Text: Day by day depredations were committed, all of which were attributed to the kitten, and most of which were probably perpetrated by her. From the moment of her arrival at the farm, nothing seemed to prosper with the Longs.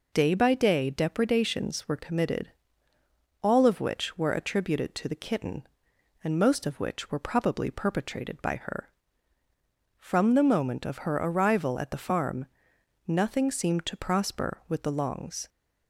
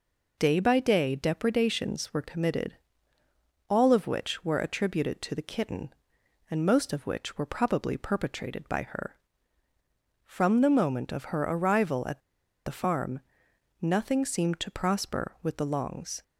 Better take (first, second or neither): first